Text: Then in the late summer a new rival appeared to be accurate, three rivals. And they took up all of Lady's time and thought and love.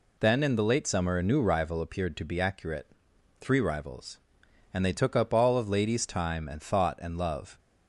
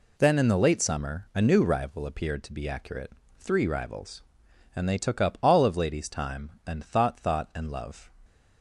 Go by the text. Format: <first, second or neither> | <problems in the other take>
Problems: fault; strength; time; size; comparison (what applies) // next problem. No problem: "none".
first | says "thought" twice; at 7.1 s